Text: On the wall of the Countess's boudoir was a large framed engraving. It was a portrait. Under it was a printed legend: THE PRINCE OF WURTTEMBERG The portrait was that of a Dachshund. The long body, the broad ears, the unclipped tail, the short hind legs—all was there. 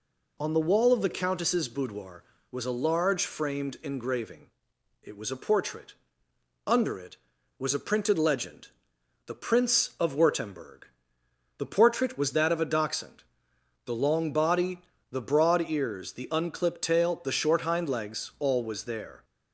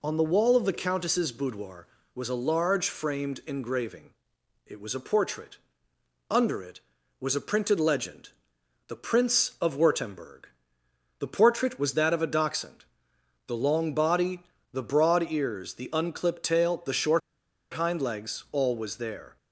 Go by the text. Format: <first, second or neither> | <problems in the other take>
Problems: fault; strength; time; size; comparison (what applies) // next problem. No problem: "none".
first | pauses between "WURTTEMBERG" and "The"; noticeable; at 10.4 s; 0.72 s long; noticeable in the first // pauses between "short" and "hind"; noticeable; at 17.2 s; 0.52 s long